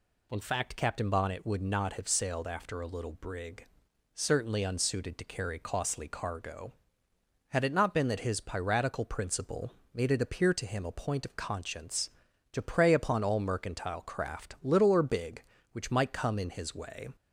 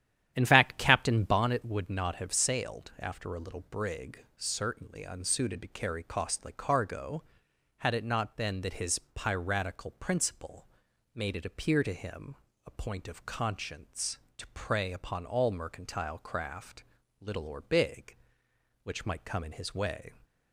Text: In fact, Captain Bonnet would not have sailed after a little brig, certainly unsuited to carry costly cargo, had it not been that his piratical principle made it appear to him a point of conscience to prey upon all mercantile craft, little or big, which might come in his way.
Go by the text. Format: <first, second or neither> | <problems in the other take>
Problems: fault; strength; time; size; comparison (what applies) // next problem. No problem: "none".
first | starts louder than the rest; strong; until 1.6 s; 10.5 dB // pauses between "principle" and "made"; noticeable; at 10.6 s; 0.46 s long; slight in the first // pauses between "him" and "a"; slight; at 12.3 s; 0.30 s long